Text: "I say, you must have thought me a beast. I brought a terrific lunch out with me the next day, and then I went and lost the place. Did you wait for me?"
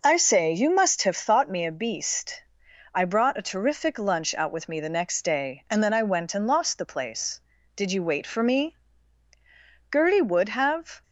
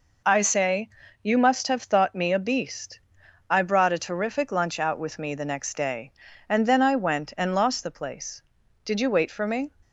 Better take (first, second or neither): second